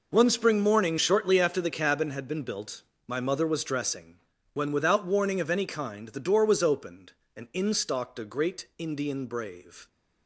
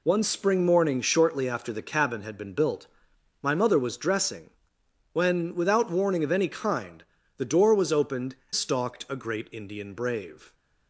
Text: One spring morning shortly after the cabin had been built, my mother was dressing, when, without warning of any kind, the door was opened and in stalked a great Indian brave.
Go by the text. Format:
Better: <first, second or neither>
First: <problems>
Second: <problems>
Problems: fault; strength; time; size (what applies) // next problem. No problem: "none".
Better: first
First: none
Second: skips "and in"; at 8.4 s